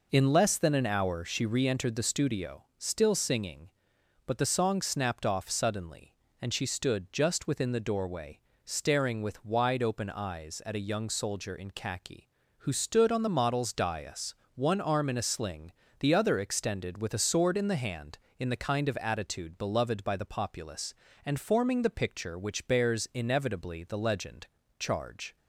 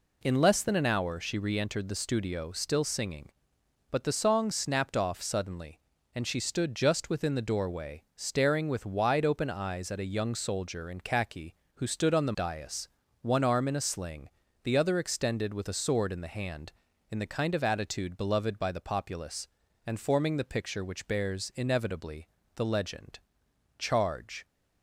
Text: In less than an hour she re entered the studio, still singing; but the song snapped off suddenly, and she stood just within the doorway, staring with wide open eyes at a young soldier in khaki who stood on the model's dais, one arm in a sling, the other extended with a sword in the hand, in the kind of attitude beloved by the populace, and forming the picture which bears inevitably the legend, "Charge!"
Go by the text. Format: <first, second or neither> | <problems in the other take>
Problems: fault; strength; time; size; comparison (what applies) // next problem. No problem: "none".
first | skips "model's"; at 12.3 s // pauses between "inevitably" and "the"; slight; at 22.2 s; 0.30 s long